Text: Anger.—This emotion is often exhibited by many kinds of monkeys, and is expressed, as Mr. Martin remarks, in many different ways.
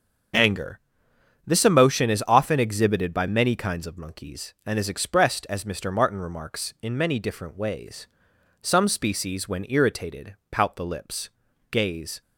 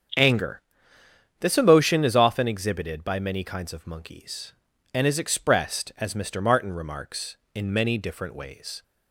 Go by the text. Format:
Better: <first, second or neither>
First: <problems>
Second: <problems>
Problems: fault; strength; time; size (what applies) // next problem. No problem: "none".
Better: second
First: starts louder than the rest; until 2.0 s; 6.5 dB // goes on to say "Some species when irritated pout the lips gaze"; strong; from 8.6 s on; 3.5 s long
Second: starts louder than the rest; strong; until 1.9 s; 7.5 dB